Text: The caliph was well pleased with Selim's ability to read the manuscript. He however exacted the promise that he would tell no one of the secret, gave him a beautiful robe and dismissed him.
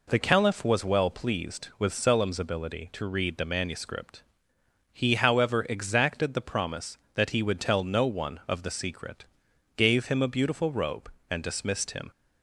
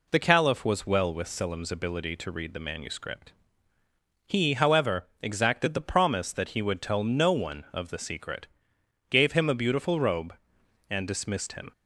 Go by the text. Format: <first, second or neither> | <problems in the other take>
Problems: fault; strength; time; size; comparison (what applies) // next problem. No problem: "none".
first | skips "pleased"; at 1.1 s // pauses between "however" and "exacted"; slight; at 5.0 s; 0.16 s long